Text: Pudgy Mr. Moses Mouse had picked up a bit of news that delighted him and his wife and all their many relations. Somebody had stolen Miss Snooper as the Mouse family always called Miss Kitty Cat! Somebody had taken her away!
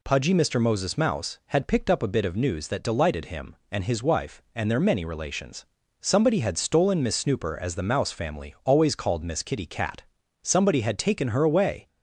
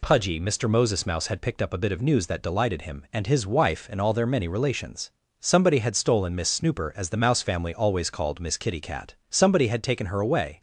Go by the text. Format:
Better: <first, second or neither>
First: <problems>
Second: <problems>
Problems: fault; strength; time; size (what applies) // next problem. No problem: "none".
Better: second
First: skips "all"; at 4.7 s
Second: none